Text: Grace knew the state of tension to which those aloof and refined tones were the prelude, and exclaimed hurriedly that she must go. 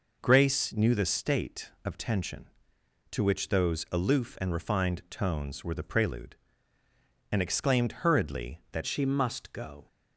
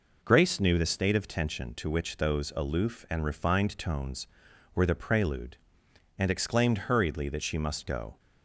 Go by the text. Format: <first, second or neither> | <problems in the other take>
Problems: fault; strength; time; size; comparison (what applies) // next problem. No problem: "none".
second | changes voice at "she"; from 8.8 s on; 1.0 s long